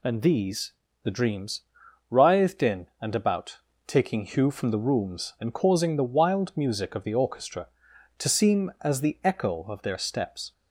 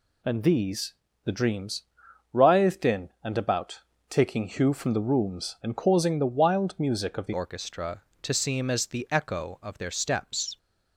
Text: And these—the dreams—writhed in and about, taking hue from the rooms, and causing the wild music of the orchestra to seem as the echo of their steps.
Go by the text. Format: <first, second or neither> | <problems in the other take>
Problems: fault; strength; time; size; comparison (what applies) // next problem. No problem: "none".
first | changes voice at "orchestra"; from 7.3 s on; 3.2 s long